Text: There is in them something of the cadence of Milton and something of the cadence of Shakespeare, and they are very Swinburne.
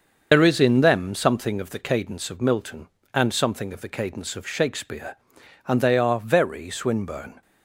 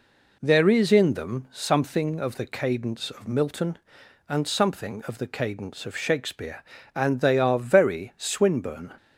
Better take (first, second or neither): second